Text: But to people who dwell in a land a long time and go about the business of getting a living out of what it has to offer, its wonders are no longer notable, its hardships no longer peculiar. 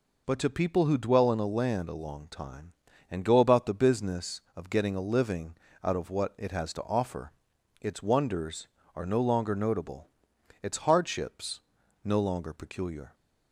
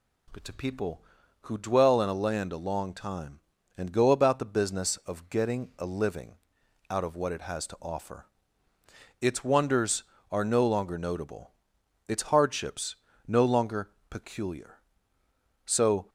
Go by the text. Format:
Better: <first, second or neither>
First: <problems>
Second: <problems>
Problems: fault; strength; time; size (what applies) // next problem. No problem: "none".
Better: first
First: pauses between "living" and "out"; slight; at 5.5 s; 0.28 s long // pauses between "hardships" and "no"; at 11.6 s; 0.44 s long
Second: pauses between "living" and "out"; noticeable; at 6.3 s; 0.56 s long // pauses between "hardships" and "no"; slight; at 12.9 s; 0.34 s long // pauses between "longer" and "peculiar"; slight; at 13.9 s; 0.18 s long // goes on to say "So"; slight; from 15.6 s on; 0.44 s long